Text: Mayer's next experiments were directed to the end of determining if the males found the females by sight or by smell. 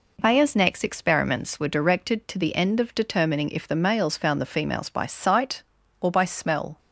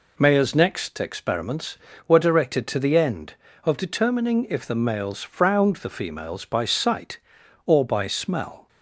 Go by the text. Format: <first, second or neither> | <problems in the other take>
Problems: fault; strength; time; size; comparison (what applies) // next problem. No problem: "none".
first | says "frowned" for "found"; at 5.2 s